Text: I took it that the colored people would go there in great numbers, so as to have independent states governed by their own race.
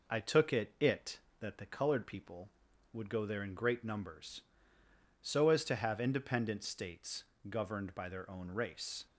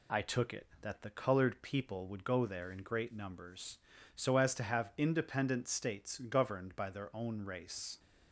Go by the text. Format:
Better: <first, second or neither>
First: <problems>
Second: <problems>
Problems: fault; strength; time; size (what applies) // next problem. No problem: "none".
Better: second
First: says "it" twice; at 0.7 s // pauses between "states" and "governed"; slight; at 7.2 s; 0.26 s long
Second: none